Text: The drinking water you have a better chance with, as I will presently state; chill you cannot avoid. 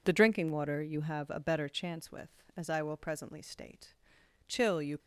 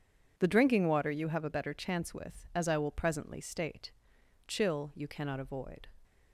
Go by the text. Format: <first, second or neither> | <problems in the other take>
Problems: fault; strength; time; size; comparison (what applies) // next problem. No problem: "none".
second | stops before "cannot avoid"; at 4.9 s